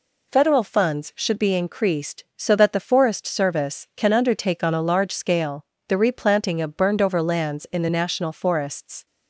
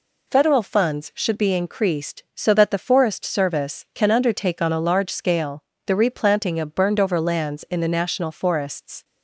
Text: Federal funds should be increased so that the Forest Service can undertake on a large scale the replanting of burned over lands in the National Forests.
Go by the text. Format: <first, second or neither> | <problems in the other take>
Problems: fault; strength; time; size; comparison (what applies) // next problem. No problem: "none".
neither | pauses between "scale" and "the"; slight; the same in both